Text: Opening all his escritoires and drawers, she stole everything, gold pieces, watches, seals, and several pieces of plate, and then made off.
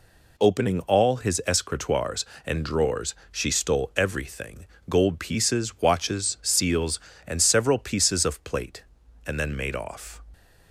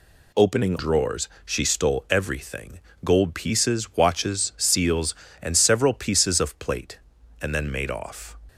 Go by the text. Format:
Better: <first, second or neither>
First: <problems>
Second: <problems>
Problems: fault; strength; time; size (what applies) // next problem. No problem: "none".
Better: first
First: none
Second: skips "all his escritoires and"; at 0.7 s